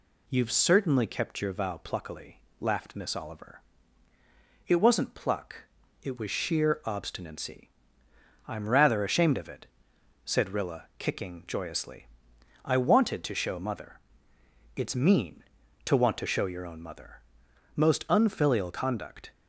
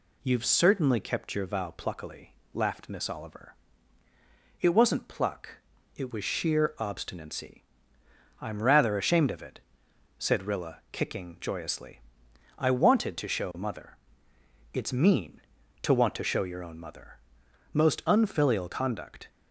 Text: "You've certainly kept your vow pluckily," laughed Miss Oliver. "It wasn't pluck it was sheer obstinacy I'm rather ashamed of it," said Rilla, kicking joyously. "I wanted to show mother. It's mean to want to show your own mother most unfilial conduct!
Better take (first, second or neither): neither